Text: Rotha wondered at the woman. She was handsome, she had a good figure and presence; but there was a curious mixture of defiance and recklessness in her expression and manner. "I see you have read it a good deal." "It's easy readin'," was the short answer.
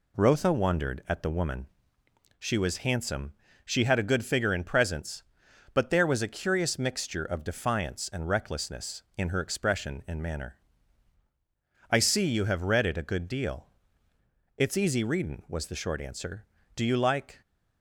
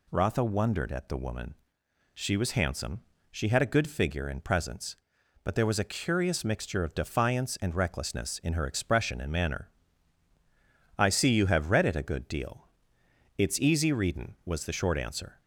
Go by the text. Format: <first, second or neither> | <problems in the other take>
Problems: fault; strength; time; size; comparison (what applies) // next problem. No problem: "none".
second | goes on to say "Do you like"; noticeable; from 16.7 s on; 0.64 s long